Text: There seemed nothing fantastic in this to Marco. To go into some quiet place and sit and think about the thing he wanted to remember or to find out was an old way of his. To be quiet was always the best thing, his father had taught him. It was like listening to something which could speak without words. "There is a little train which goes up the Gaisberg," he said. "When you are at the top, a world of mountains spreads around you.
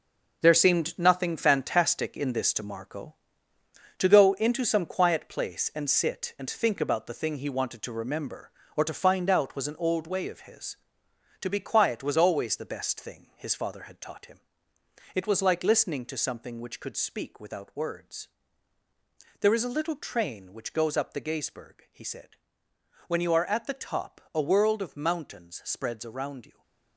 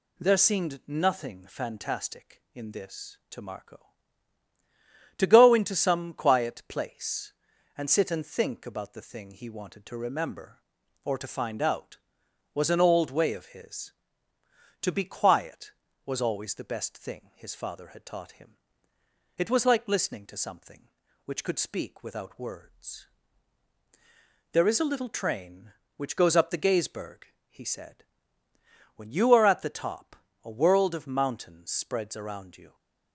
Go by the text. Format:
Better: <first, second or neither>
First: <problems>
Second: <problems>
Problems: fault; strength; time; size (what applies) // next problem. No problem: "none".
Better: second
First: gets quieter; strong; throughout; 9 dB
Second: none